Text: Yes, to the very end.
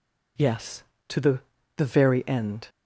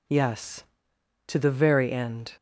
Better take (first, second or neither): second